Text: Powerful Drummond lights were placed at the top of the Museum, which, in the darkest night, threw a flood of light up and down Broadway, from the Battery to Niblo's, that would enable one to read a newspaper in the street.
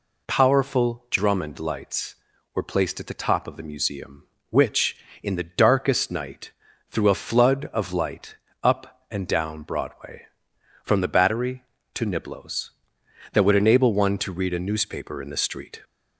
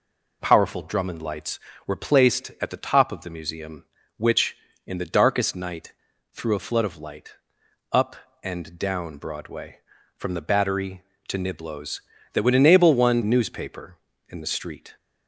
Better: first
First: pauses between "light" and "up"; slight; at 8.3 s; 0.28 s long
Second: pauses between "light" and "up"; noticeable; at 7.3 s; 0.58 s long // skips "to read a"; at 13.2 s

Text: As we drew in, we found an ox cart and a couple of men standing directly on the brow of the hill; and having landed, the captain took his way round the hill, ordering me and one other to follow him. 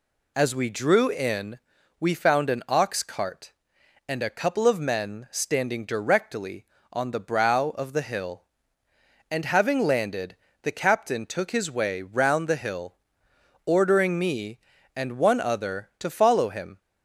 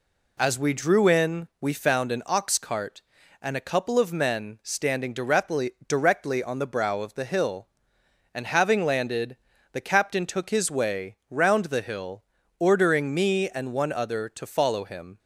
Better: first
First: none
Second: says "directly" twice; at 5.8 s

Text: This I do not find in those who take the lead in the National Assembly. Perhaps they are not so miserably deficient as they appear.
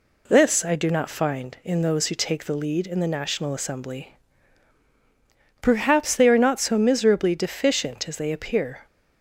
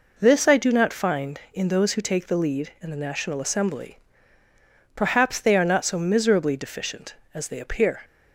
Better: neither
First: none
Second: none

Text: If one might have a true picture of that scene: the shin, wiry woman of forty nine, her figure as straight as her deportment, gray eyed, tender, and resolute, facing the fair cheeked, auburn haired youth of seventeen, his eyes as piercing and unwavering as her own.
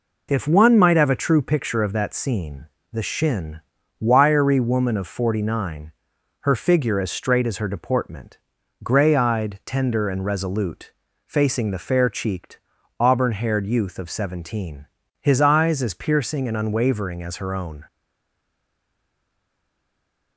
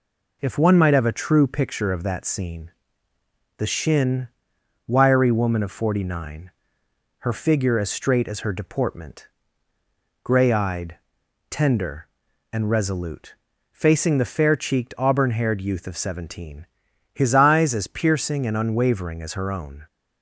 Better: second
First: stays silent after the last word; from 17.8 s on; 2.5 s long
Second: none

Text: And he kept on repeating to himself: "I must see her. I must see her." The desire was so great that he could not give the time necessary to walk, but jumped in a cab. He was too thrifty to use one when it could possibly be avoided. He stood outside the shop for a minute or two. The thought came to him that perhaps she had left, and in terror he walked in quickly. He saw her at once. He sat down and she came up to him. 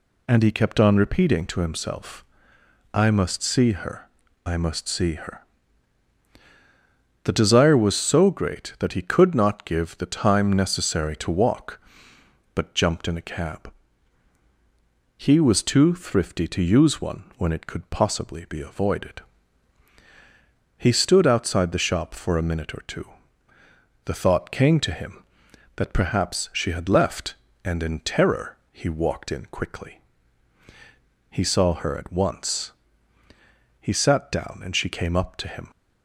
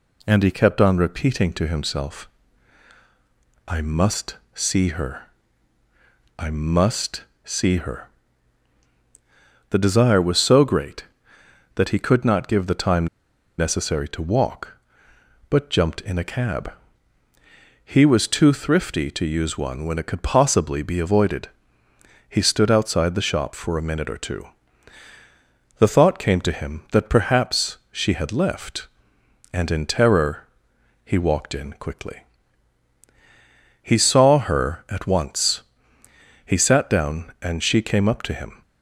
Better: first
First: none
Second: pauses between "must" and "see"; slight; at 4.3 s; 0.18 s long // pauses between "must" and "see"; slight; at 7.2 s; 0.20 s long // pauses between "time" and "necessary"; noticeable; at 13.0 s; 0.52 s long // pauses between "terror" and "he"; noticeable; at 30.4 s; 0.56 s long

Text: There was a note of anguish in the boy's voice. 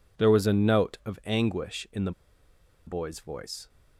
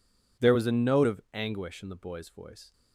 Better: second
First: pauses between "the" and "boy's"; noticeable; at 2.1 s; 0.75 s long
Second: none

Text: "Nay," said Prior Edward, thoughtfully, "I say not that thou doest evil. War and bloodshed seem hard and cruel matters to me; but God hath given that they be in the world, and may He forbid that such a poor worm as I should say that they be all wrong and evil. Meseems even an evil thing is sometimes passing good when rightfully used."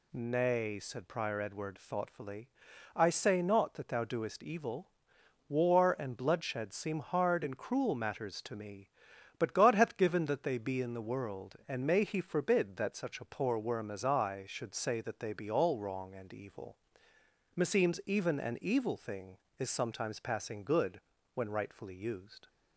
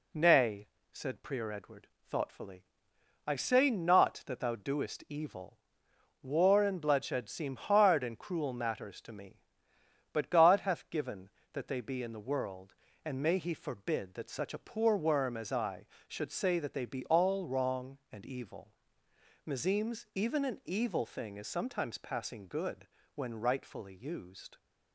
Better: neither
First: pauses between "good" and "when"; slight; at 20.9 s; 0.34 s long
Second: pauses between "good" and "when"; slight; at 22.8 s; 0.30 s long

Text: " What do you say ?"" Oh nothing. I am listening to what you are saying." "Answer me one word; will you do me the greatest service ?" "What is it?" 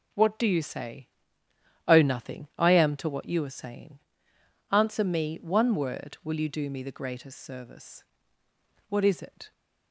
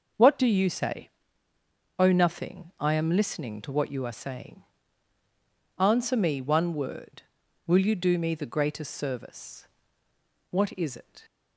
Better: second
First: skips "listening"; at 2.9 s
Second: none

